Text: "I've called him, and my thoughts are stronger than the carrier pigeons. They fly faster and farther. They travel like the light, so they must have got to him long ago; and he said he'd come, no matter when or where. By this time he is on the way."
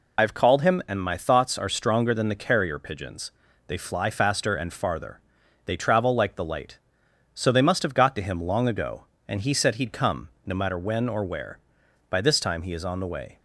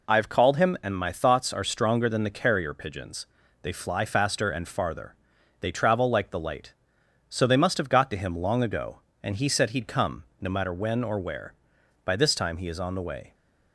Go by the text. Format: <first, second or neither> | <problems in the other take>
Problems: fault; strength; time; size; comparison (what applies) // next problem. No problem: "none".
second | loses the start of "I've"; at 0.1 s; 55 ms